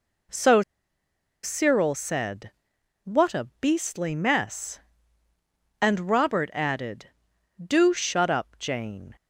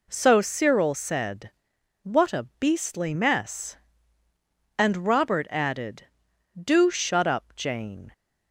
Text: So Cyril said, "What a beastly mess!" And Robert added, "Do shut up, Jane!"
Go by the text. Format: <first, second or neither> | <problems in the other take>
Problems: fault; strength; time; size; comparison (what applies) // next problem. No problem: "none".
second | pauses between "So" and "Cyril"; noticeable; at 0.6 s; 0.82 s long